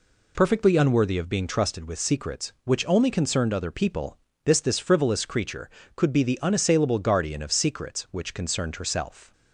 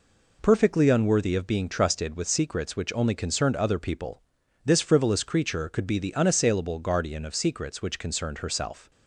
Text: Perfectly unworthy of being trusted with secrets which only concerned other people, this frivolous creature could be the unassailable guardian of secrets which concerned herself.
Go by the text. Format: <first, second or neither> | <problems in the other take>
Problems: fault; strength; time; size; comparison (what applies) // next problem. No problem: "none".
second | says "this" twice; at 4.5 s